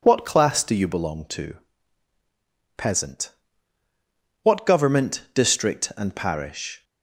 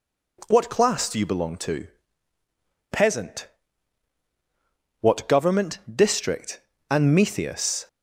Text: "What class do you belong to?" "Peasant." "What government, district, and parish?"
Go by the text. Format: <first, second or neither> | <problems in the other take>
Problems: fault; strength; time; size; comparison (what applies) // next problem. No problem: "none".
first | says "metheus" for "parish"; at 7.1 s